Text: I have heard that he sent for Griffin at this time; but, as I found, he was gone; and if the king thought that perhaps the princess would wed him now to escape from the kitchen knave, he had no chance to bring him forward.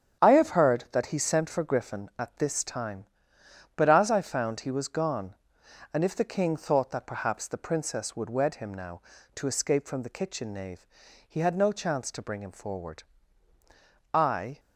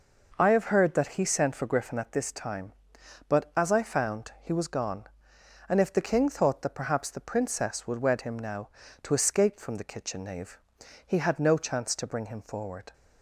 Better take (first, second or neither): second